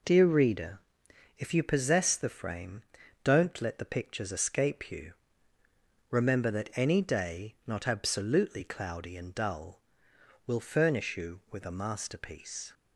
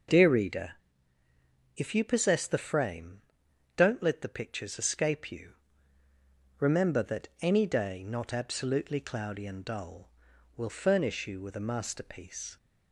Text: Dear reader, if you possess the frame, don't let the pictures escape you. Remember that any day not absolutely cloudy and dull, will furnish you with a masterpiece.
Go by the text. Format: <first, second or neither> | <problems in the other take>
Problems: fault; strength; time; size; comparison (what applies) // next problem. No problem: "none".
neither | none